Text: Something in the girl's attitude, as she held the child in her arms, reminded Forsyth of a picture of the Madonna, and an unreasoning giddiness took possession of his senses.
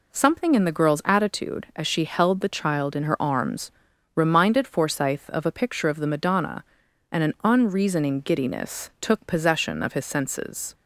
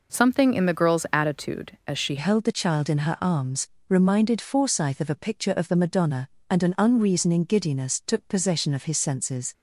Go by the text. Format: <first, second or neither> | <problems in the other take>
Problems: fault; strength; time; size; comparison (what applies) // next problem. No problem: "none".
first | changes voice at "held"; from 2.1 s on; 7.4 s long